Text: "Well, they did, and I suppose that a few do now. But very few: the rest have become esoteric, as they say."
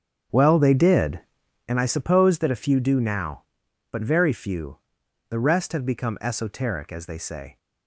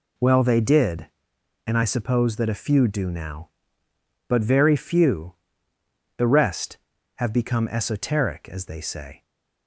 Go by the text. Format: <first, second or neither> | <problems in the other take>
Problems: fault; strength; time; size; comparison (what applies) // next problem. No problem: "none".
second | starts louder than the rest; strong; until 1.7 s; 7.5 dB